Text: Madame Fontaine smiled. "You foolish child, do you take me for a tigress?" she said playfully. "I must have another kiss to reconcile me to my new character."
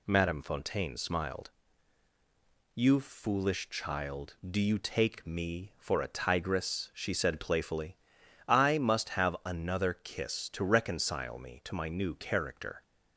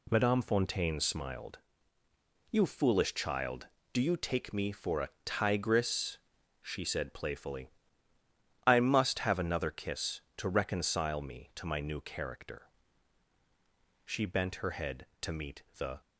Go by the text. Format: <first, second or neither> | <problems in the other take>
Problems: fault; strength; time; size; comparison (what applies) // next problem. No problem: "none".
first | pauses between "a" and "tigress"; slight; at 5.1 s; 0.16 s long // goes on to say "She bent her head to meet the"; strong; from 14.0 s on; 1.9 s long